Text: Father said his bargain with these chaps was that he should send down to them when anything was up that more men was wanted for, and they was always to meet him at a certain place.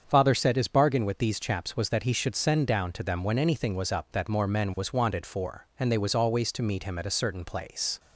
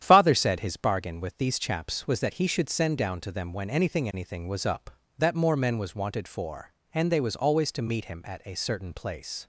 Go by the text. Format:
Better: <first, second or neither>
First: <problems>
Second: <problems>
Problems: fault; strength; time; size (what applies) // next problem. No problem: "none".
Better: first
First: starts louder than the rest; strong; until 1.1 s; 7.5 dB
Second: starts louder than the rest; strong; until 1.0 s; 10 dB // says "anything" twice; at 4.1 s